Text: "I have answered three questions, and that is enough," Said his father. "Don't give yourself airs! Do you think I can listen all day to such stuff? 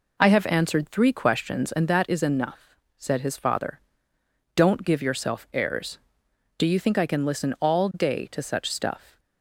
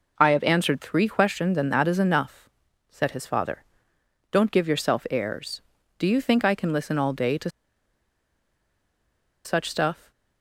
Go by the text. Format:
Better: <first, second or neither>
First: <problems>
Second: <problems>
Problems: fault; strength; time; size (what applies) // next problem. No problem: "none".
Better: first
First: none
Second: pauses between "to" and "such"; strong; at 7.4 s; 1.9 s long